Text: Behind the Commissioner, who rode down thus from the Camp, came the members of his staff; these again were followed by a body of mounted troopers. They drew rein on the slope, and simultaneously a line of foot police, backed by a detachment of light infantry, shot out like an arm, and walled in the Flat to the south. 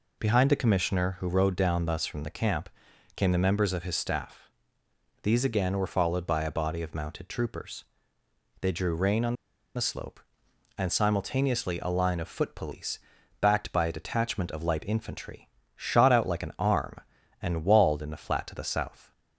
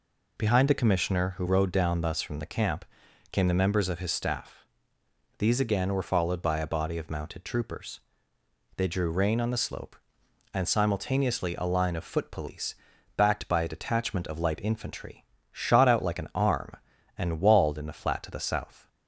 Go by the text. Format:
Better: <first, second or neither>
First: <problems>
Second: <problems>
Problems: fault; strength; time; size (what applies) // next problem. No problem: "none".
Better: second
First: pauses between "on" and "the"; at 9.3 s; 0.40 s long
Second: none